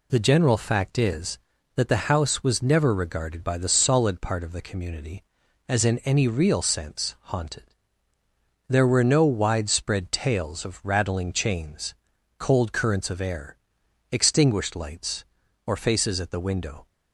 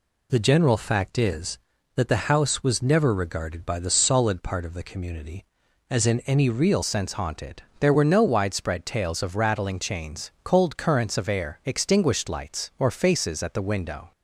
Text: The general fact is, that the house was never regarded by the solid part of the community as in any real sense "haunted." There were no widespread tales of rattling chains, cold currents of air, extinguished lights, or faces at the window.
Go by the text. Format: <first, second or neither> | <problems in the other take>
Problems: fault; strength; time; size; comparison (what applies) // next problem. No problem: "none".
first | changes voice at "sense"; from 6.8 s on; 7.3 s long